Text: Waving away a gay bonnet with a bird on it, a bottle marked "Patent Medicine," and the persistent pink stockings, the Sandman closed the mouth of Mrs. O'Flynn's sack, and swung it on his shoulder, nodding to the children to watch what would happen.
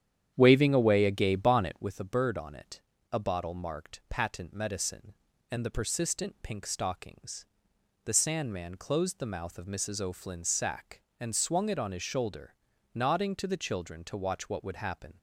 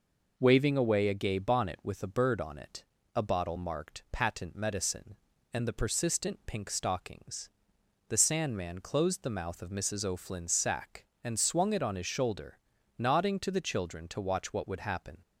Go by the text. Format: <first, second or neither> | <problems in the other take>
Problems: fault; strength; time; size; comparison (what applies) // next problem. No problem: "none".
second | starts louder than the rest; strong; until 1.9 s; 9.5 dB